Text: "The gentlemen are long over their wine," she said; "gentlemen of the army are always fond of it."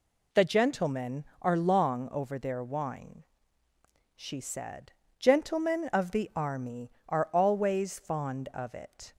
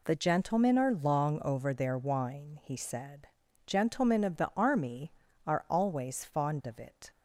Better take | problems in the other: first | says "he" for "she"; at 2.6 s

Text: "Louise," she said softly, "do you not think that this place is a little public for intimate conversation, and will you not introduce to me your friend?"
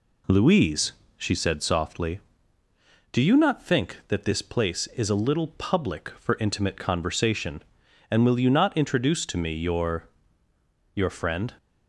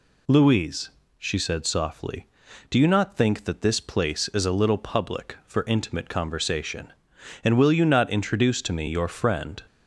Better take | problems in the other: second | says "your" twice; at 10.9 s

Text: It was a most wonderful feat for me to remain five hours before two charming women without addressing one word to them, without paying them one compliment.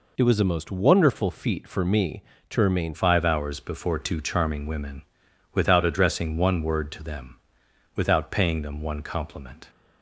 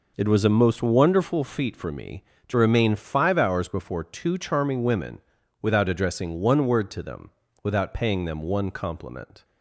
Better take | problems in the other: second | changes voice at "five"; from 2.9 s on; 6.7 s long // pauses between "women" and "without"; noticeable; at 5.0 s; 0.50 s long; also in the second

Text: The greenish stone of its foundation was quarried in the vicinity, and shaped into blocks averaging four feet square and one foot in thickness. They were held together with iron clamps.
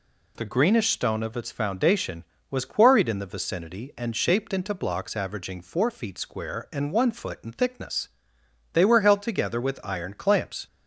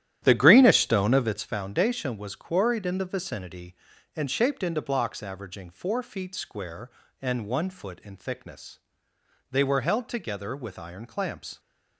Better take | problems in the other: first | starts louder than the rest; strong; until 1.5 s; 11.5 dB

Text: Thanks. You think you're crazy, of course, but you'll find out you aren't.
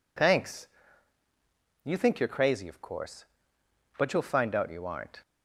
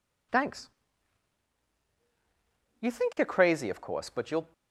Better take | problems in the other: first | stops before "find out you aren't"; at 4.5 s

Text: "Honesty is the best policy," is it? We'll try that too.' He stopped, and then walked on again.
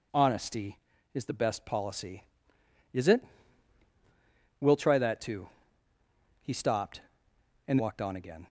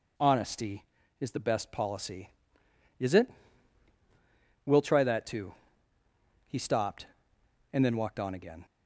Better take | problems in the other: second | skips "then"; at 7.7 s

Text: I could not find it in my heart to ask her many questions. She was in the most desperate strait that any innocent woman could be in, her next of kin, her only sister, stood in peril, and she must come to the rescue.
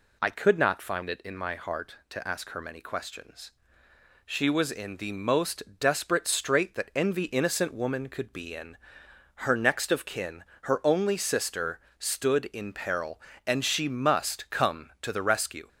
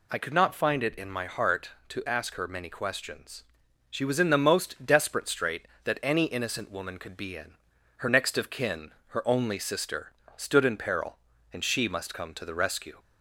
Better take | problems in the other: second | pauses between "most" and "desperate"; slight; at 5.6 s; 0.16 s long // says "envy" for "any"; at 6.9 s

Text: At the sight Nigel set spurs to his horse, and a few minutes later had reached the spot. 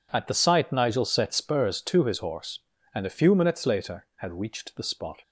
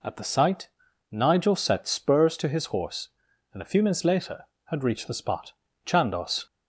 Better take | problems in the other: first | pauses between "sight" and "Nigel"; at 0.6 s; 0.42 s long // goes on to say "Chandos"; from 5.8 s on; 0.60 s long

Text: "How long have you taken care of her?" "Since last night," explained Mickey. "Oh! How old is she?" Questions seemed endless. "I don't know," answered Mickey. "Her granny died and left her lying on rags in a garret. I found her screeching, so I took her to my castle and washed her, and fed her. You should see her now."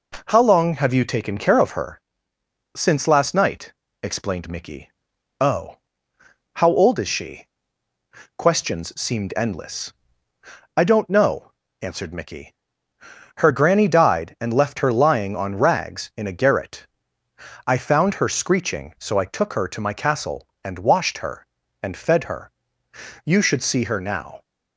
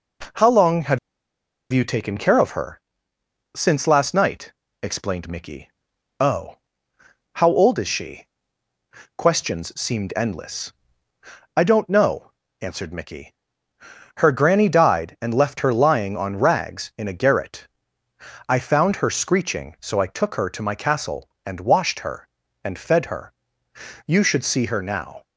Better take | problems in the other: first | pauses between "have" and "you"; noticeable; at 0.9 s; 0.74 s long

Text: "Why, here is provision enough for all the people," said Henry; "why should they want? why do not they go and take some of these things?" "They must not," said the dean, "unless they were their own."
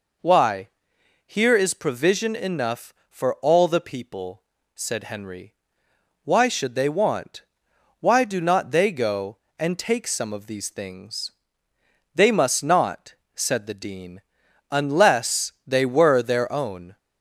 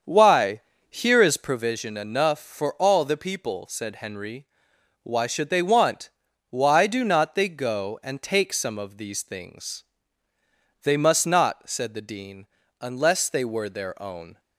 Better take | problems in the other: first | starts louder than the rest; until 1.7 s; 7 dB

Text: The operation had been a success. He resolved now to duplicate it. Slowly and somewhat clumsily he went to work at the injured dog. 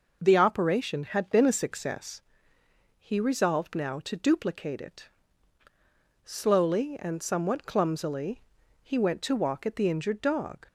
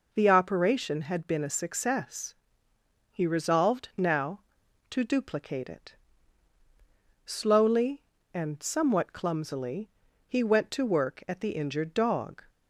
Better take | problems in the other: second | pauses between "clumsily" and "he"; at 8.4 s; 0.42 s long; also in the second // says "walk" for "work"; at 9.3 s

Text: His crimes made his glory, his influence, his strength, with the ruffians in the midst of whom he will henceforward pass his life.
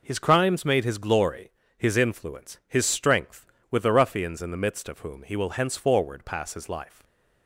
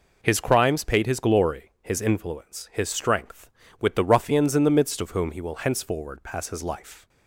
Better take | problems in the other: first | says "paid" for "made"; at 0.8 s

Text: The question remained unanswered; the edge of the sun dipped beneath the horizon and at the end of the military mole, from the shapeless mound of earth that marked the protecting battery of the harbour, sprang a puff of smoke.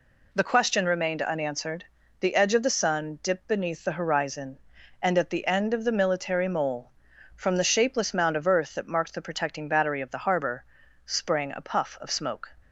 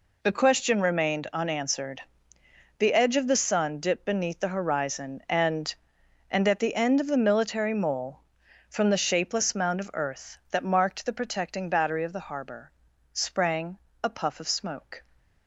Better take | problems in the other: first | says "and" twice; at 6.2 s // pauses between "sprang" and "a"; slight; at 13.7 s; 0.24 s long

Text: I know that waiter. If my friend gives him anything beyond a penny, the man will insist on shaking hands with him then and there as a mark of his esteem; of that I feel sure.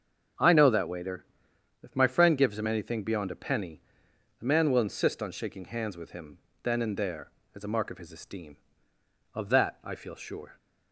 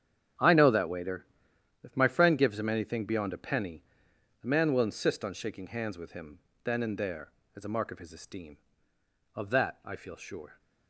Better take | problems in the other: first | gets quieter; strong; throughout; 13.5 dB // starts louder than the rest; strong; until 1.9 s; 8.5 dB; also in the first // pauses between "him" and "then"; slight; at 6.4 s; 0.24 s long; slight in the first

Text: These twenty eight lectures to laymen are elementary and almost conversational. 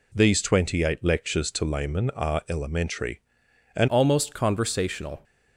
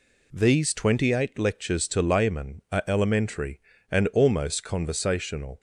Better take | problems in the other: second | changes voice at "almost"; from 3.8 s on; 1.4 s long

